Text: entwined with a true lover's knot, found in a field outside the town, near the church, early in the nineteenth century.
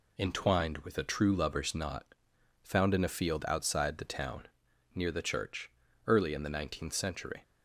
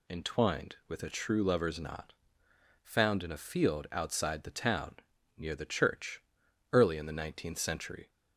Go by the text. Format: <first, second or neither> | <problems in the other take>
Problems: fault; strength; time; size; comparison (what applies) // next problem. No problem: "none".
second | gets quieter; noticeable; throughout; 4.5 dB